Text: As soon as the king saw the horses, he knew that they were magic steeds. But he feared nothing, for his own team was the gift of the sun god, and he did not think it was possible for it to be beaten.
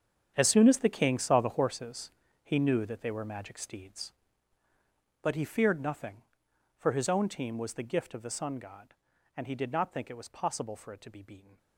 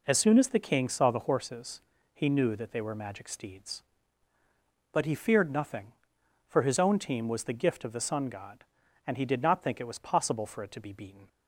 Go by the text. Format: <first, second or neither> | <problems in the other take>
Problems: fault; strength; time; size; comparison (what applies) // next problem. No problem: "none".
second | gets quieter; strong; throughout; 14.5 dB